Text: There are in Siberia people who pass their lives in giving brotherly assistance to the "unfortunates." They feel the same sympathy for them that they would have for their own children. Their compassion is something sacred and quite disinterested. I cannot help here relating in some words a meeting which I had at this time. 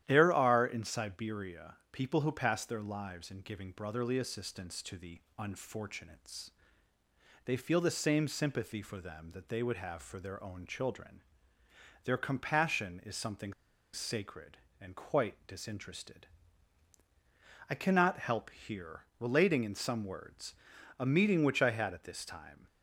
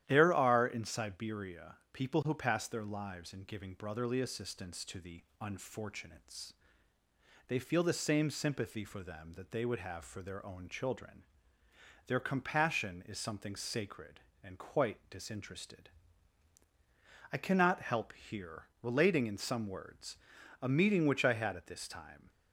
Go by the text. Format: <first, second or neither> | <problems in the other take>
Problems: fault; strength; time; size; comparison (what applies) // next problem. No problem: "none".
second | starts louder than the rest; strong; until 1.0 s; 11.5 dB; strong in the second // pauses between "Siberia" and "people"; slight; at 1.7 s; 0.18 s long; slight in the second // pauses between "the" and "unfortunates"; slight; at 5.2 s; 0.16 s long; slight in the second // pauses between "something" and "sacred"; at 13.5 s; 0.39 s long // pauses between "here" and "relating"; slight; at 19.0 s; 0.16 s long; slight in the second // pauses between "words" and "a"; at 20.5 s; 0.44 s long; also in the second